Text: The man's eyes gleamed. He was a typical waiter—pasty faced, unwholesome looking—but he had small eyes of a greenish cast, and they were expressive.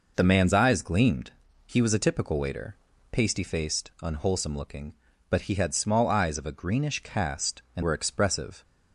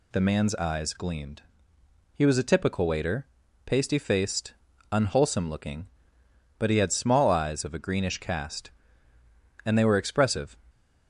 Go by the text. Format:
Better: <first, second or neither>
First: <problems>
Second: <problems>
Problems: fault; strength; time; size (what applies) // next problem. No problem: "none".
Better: second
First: skips "they"; at 7.8 s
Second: none